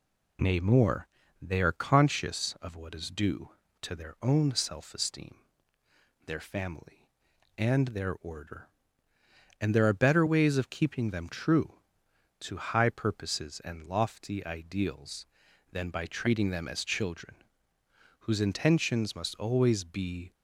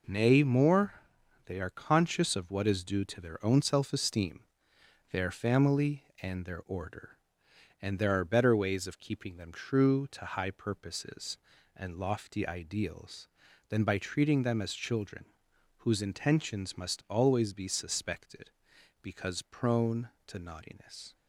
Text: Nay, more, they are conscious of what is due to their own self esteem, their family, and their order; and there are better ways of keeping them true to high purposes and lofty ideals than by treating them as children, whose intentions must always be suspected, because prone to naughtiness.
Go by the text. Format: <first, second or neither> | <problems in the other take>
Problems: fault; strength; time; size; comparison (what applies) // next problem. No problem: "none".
second | stops before "suspected because prone to naughtiness"; at 20.3 s